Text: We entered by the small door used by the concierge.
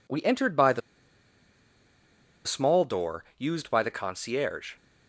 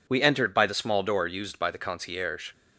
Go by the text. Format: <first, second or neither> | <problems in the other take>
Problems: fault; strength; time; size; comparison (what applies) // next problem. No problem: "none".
second | pauses between "the" and "small"; strong; at 0.8 s; 1.6 s long